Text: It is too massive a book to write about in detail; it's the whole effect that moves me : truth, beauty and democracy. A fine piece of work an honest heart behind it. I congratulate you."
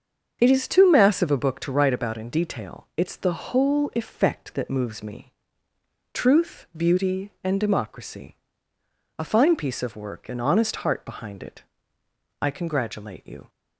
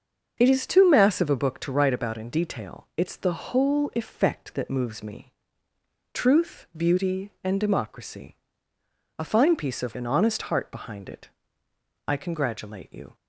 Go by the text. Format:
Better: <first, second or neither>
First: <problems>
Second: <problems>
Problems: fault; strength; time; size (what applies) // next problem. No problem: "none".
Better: first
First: starts louder than the rest; until 1.4 s; 7 dB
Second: starts louder than the rest; until 1.3 s; 6.5 dB // skips "work"; at 9.9 s